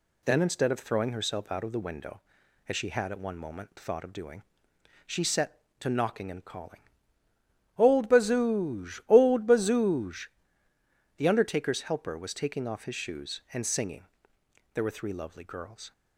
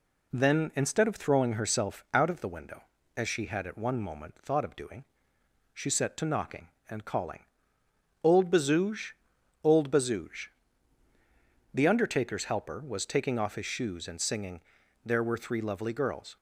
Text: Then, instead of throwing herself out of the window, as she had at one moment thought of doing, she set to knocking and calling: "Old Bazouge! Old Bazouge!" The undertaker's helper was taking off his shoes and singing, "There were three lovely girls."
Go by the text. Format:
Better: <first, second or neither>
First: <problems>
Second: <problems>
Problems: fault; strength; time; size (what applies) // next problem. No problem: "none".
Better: neither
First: none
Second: none